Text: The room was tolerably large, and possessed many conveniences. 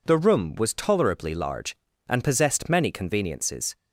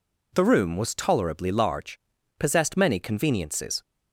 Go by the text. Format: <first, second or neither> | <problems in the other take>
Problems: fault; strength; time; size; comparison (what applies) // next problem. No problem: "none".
first | skips "and"; at 2.1 s